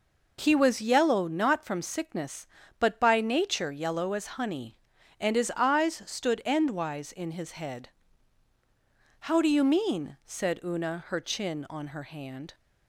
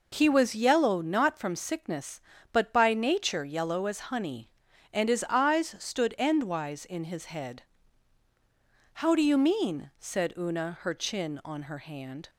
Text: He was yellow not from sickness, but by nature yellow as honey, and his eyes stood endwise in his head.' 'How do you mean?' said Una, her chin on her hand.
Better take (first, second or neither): neither